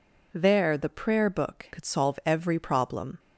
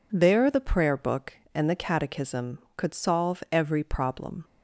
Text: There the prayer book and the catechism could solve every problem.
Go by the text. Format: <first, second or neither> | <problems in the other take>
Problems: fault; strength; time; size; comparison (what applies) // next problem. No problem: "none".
second | skips "and the catechism"; at 1.7 s